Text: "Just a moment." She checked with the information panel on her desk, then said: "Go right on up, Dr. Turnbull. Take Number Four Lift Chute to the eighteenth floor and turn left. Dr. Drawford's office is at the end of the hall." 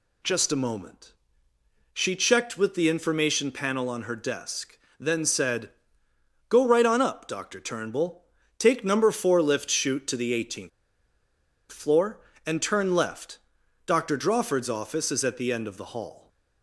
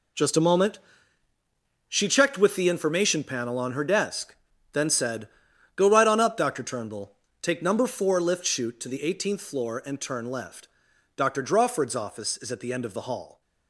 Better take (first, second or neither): second